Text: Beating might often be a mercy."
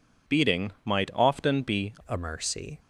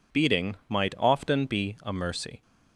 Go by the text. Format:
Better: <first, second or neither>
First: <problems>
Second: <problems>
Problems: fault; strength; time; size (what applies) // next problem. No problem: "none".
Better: second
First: changes voice at "a"; from 2.0 s on; 0.7 s long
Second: none